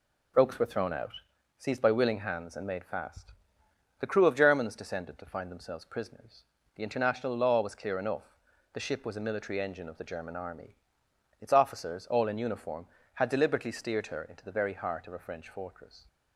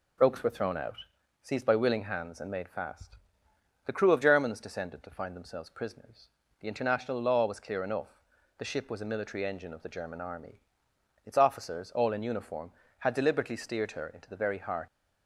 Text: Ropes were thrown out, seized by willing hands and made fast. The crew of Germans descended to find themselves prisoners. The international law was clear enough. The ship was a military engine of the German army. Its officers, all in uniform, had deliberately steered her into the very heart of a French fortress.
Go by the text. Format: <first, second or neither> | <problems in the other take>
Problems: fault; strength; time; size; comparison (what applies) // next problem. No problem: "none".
first | stops before "of a French fortress"; at 14.8 s